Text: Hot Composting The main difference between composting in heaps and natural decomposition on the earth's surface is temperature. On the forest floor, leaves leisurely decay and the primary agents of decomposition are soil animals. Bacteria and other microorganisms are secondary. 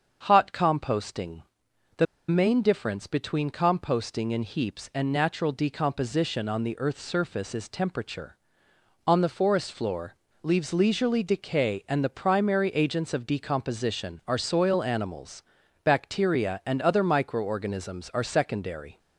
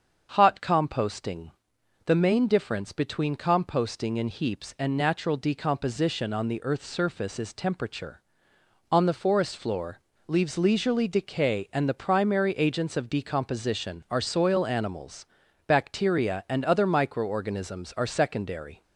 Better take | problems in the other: second | starts louder than the rest; until 1.2 s; 7 dB; also in the second // pauses between "Composting" and "The"; noticeable; at 1.4 s; 0.56 s long; noticeable in the second // pauses between "The" and "main"; slight; at 2.0 s; 0.23 s long

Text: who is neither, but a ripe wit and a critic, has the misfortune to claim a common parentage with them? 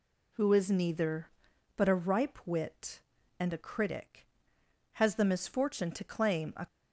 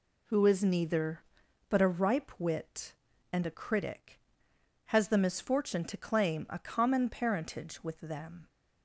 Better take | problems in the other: second | stops before "common parentage with them"; at 6.6 s

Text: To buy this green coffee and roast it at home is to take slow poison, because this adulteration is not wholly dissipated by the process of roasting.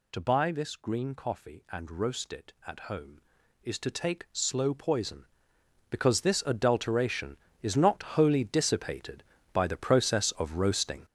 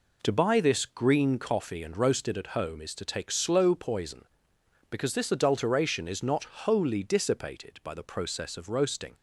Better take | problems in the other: second | gets louder; strong; throughout; 9 dB

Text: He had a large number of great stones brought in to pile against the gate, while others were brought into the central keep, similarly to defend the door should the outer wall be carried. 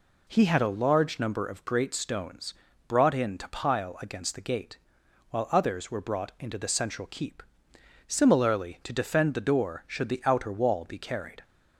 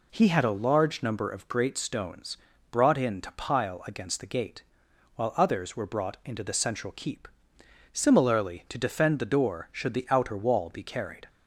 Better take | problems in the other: neither | pauses between "stones" and "brought"; slight; the same in both

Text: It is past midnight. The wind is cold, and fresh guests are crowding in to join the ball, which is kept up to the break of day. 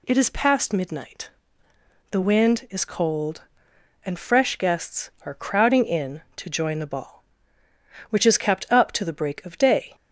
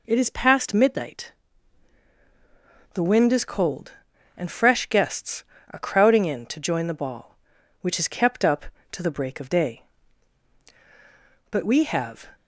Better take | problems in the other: first | goes on to say "But we have"; noticeable; from 11.5 s on; 0.81 s long

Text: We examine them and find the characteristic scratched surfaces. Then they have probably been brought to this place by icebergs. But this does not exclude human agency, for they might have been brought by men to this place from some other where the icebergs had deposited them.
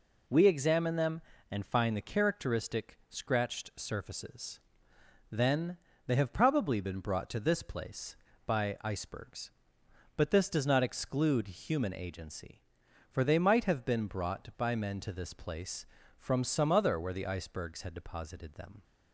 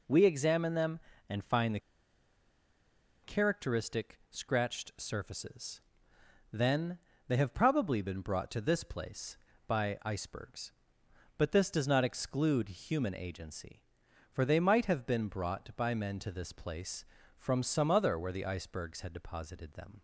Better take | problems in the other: first | pauses between "the" and "characteristic"; strong; at 1.7 s; 1.4 s long // pauses between "Then" and "they"; slight; at 6.9 s; 0.30 s long; slight in the first

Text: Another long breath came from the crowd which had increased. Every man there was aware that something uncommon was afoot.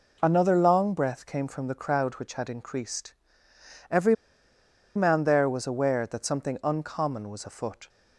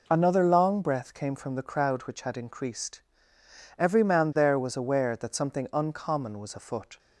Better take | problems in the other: second | pauses between "Every" and "man"; noticeable; at 4.1 s; 0.81 s long

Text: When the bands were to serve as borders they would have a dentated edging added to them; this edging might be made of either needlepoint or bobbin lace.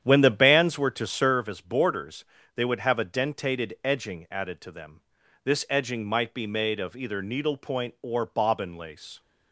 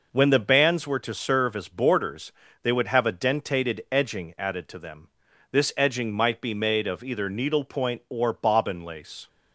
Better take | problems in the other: second | starts louder than the rest; strong; until 1.5 s; 9.5 dB // pauses between "borders" and "they"; slight; at 2.2 s; 0.30 s long; slight in the second

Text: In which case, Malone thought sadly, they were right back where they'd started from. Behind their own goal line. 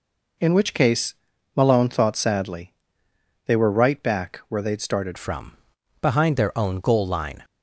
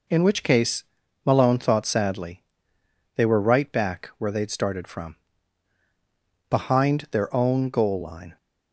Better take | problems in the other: second | changes voice at "from"; from 5.1 s on; 2.3 s long

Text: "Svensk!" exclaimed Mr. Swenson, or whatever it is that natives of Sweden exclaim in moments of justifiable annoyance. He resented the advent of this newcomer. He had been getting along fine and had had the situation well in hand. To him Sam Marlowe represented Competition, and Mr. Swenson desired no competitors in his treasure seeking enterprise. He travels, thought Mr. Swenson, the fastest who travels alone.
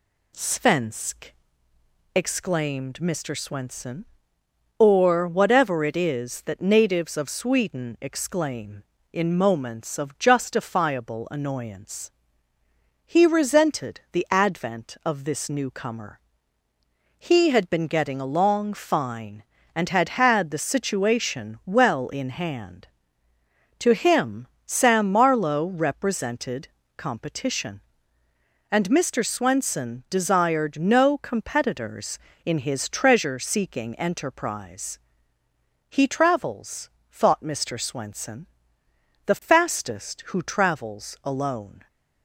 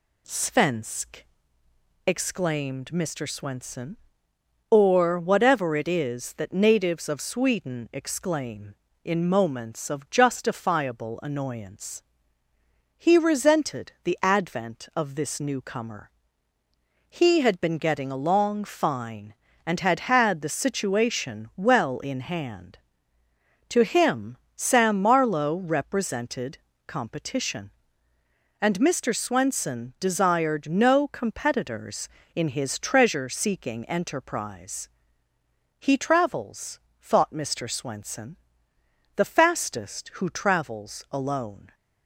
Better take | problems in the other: neither | pauses between "him" and "Sam"; slight; the same in both // pauses between "represented" and "Competition"; slight; the same in both

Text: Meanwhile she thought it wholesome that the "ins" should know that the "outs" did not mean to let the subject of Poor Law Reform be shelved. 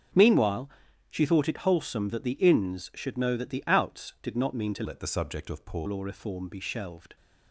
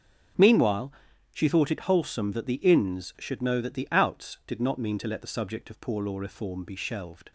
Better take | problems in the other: second | starts louder than the rest; until 1.5 s; 6.5 dB; also in the second // pauses between "Meanwhile" and "she"; at 0.6 s; 0.40 s long; also in the second // changes voice from "let" to "Poor"; from 4.8 to 5.8 s; 1.0 s long

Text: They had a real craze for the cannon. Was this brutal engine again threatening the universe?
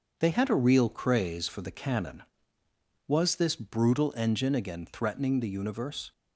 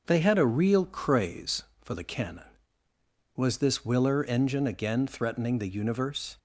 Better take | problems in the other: first | starts louder than the rest; noticeable; until 1.0 s; 6 dB; also in the first // says "willer" for "brutal"; at 3.8 s

